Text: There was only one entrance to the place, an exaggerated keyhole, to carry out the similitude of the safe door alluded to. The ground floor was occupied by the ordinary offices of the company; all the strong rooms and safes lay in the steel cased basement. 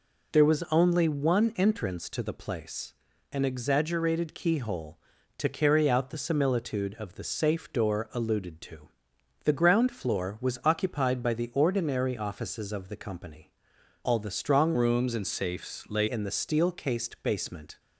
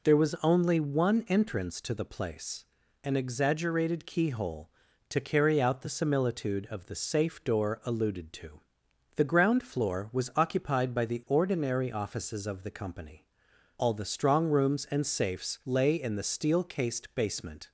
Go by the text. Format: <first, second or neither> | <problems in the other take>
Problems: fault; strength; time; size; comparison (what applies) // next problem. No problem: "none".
second | changes voice from "rooms" to "lay"; from 14.7 to 16.0 s; 1.3 s long